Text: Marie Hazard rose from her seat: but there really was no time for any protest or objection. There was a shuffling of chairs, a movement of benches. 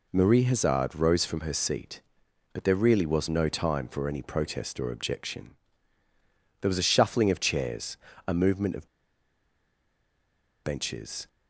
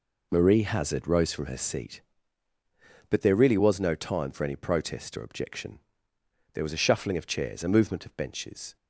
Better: second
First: pauses between "of" and "benches"; strong; at 8.8 s; 1.7 s long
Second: none

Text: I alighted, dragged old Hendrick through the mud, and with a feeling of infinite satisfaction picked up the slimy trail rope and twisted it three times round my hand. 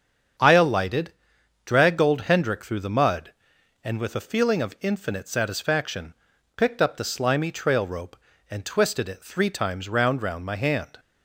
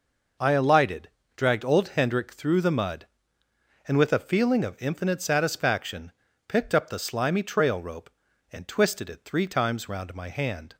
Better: second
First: starts louder than the rest; strong; until 1.9 s; 7.5 dB // pauses between "satisfaction" and "picked"; at 6.1 s; 0.44 s long // says "round" twice; at 10.2 s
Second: pauses between "satisfaction" and "picked"; slight; at 6.1 s; 0.36 s long

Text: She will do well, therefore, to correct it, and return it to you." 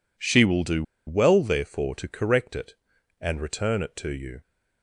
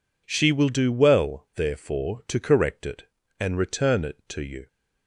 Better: second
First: pauses between "do" and "well"; slight; at 0.8 s; 0.24 s long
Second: none

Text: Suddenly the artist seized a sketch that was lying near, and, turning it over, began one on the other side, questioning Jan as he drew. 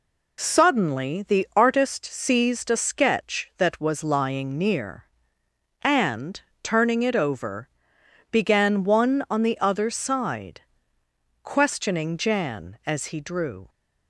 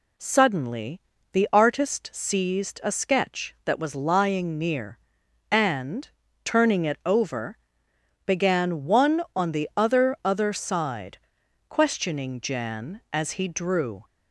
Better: first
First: none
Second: pauses between "Suddenly" and "the"; slight; at 1.0 s; 0.32 s long // says "other" twice; at 10.2 s

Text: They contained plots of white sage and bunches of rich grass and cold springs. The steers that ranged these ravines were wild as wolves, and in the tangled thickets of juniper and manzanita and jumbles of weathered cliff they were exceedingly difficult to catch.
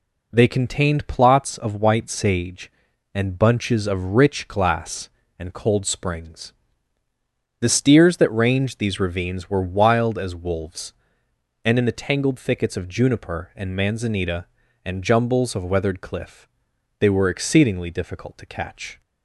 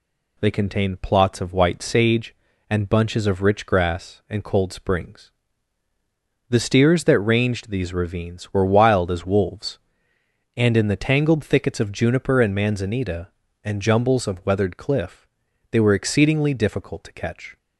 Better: second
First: says "glass" for "grass"; at 4.4 s // pauses between "cliff" and "they"; noticeable; at 16.4 s; 0.54 s long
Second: pauses between "cliff" and "they"; at 15.2 s; 0.44 s long

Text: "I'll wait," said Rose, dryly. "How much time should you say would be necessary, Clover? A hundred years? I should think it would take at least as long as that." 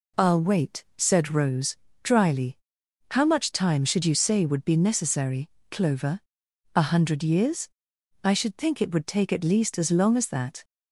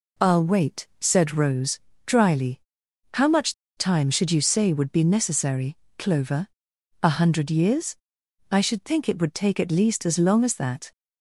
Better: first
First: none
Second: pauses between "much" and "time"; slight; at 3.5 s; 0.22 s long

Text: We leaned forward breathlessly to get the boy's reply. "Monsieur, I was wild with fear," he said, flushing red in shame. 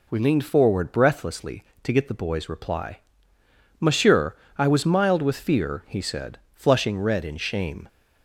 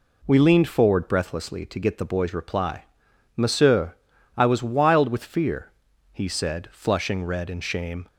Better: second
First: says "mild" for "wild"; at 4.8 s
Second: none

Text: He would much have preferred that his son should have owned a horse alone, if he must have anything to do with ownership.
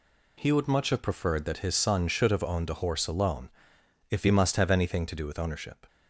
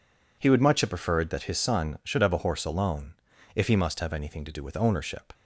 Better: first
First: none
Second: skips "owned"; at 2.3 s

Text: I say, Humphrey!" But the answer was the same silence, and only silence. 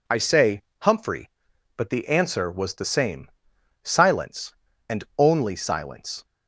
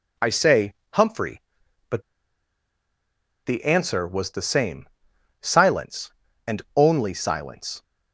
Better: first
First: pauses between "same" and "silence"; noticeable; at 3.3 s; 0.54 s long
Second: pauses between "But" and "the"; strong; at 2.0 s; 1.4 s long // pauses between "same" and "silence"; noticeable; at 4.8 s; 0.54 s long

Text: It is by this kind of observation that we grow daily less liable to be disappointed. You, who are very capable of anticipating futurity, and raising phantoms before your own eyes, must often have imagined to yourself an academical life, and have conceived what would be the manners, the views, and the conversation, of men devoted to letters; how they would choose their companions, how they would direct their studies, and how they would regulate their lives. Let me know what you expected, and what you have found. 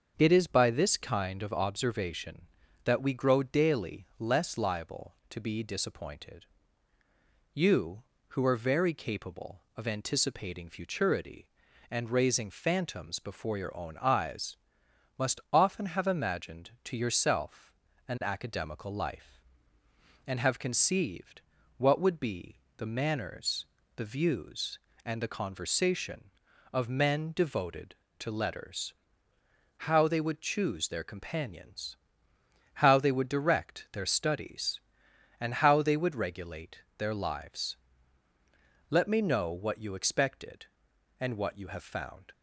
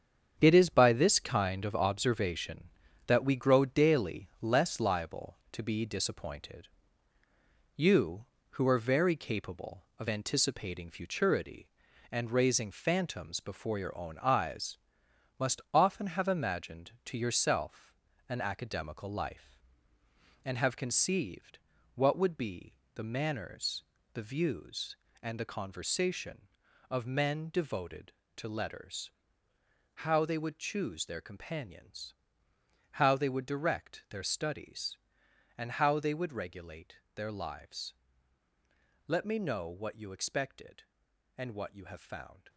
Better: first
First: starts louder than the rest; until 1.1 s; 6.5 dB // pauses between "yourself" and "an"; slight; at 17.7 s; 0.34 s long // pauses between "conceived" and "what"; slight; at 21.4 s; 0.36 s long // pauses between "be" and "the"; slight; at 22.5 s; 0.22 s long // pauses between "regulate" and "their"; slight; at 36.7 s; 0.18 s long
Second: gets quieter; strong; throughout; 8 dB // starts louder than the rest; strong; until 1.3 s; 7.5 dB // pauses between "yourself" and "an"; slight; at 17.9 s; 0.34 s long // pauses between "conceived" and "what"; slight; at 21.5 s; 0.36 s long // pauses between "be" and "the"; slight; at 22.7 s; 0.22 s long // pauses between "regulate" and "their"; slight; at 36.9 s; 0.18 s long

